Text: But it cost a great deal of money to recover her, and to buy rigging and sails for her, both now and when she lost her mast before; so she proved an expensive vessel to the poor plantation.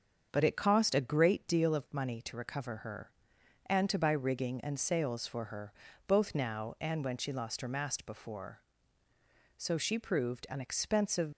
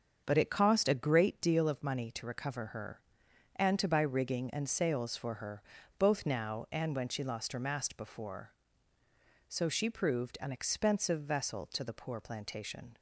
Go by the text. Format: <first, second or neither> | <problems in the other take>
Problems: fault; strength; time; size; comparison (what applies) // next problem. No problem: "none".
second | starts louder than the rest; until 1.3 s; 7 dB; also in the second // stops before "vessel to the poor plantation"; at 11.3 s